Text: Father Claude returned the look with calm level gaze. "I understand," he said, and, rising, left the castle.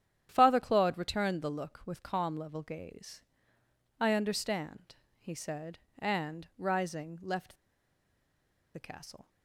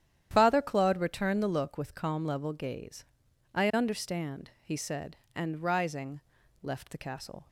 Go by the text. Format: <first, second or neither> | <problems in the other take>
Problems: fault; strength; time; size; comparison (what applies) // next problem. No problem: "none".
second | starts louder than the rest; strong; until 1.3 s; 10 dB; strong in the second // pauses between "left" and "the"; at 7.5 s; 1.1 s long